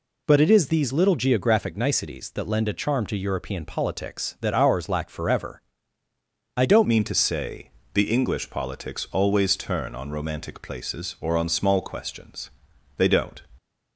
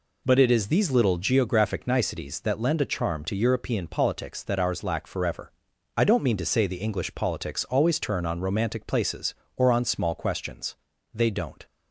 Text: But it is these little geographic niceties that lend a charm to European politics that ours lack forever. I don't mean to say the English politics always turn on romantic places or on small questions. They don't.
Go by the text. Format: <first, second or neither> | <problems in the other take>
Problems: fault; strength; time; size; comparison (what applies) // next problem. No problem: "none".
second | changes voice at "mean"; from 6.8 s on; 6.6 s long // pauses between "say" and "the"; slight; at 7.6 s; 0.24 s long